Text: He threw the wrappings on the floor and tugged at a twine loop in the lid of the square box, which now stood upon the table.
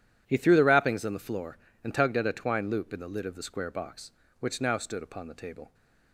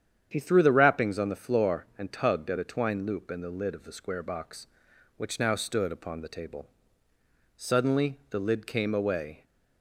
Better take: first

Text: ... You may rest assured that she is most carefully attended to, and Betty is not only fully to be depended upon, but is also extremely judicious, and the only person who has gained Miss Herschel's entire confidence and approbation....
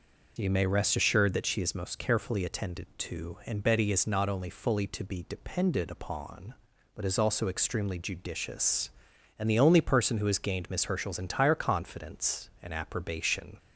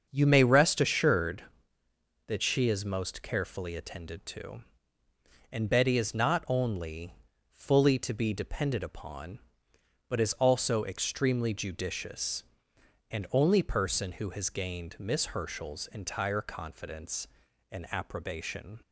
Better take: first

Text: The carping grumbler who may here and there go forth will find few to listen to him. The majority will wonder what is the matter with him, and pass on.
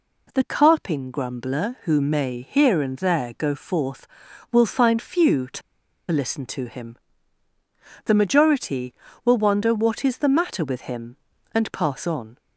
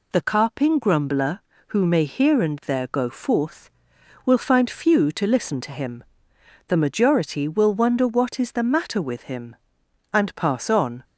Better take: second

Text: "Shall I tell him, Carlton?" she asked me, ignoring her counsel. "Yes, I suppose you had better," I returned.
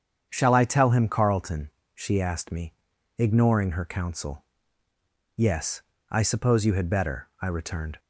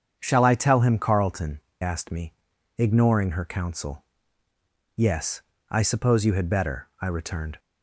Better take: first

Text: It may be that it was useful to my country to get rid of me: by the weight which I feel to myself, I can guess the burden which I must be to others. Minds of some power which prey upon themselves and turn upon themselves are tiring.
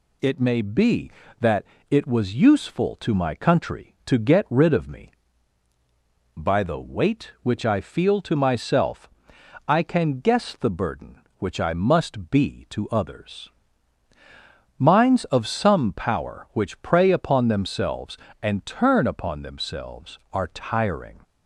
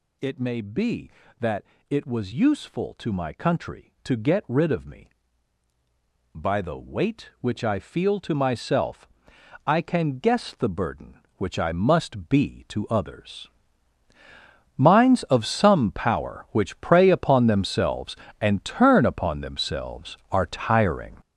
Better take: first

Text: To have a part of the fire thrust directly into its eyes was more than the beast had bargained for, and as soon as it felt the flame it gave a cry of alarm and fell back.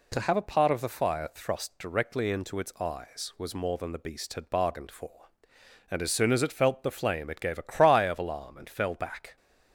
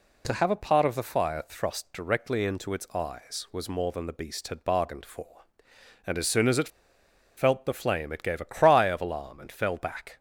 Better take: first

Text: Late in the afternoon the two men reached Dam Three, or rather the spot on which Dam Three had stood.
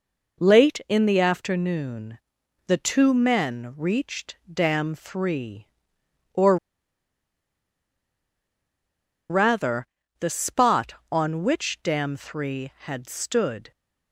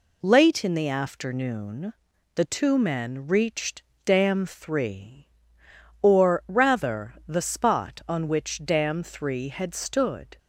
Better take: second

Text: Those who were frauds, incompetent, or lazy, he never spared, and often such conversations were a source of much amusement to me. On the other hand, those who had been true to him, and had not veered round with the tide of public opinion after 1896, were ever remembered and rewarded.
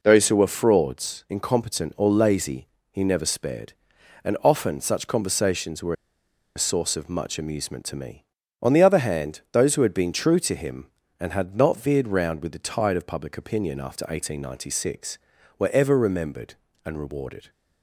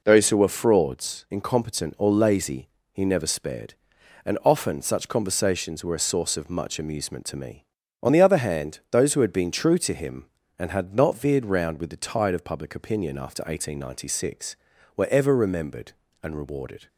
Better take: second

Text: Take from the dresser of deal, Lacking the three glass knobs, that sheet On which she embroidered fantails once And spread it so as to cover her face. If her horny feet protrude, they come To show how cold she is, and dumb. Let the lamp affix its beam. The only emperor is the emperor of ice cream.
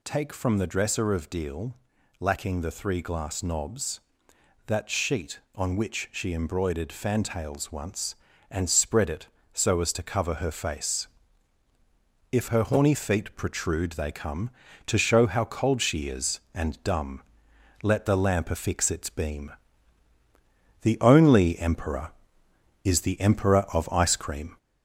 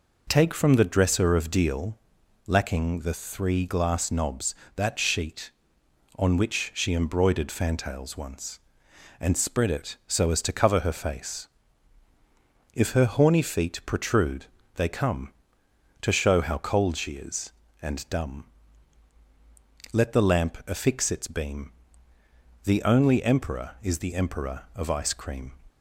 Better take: second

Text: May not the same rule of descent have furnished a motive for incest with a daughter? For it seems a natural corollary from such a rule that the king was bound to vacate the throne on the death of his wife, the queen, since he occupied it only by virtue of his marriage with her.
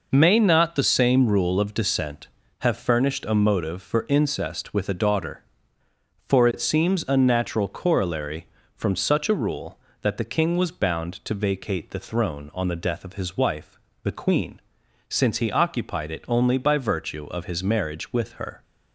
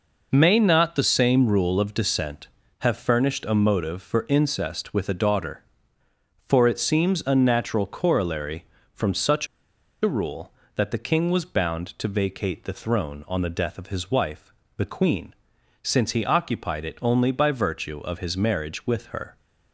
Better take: first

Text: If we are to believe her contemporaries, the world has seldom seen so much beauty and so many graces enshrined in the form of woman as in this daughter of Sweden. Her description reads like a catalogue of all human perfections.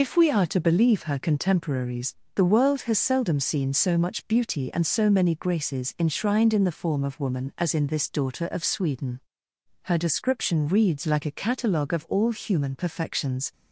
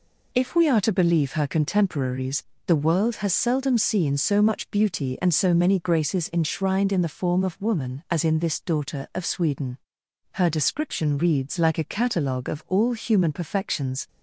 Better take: second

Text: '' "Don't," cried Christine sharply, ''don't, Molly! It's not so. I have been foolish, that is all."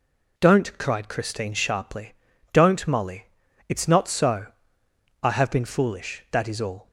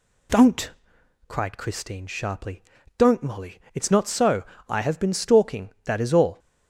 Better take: first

